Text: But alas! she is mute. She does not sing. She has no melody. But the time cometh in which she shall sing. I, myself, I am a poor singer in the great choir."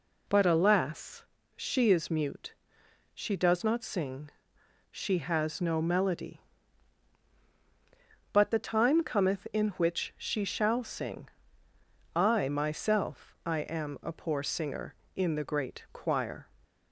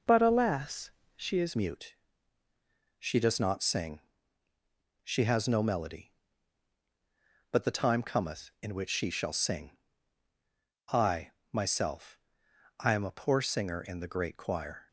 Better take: first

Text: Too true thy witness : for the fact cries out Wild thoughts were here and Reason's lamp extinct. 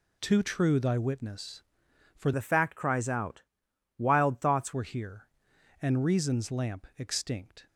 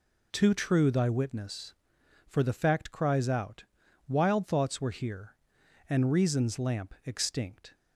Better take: second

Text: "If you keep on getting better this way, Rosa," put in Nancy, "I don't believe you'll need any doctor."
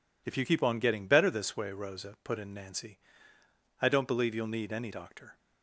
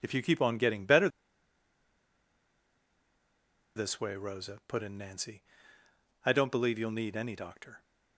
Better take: first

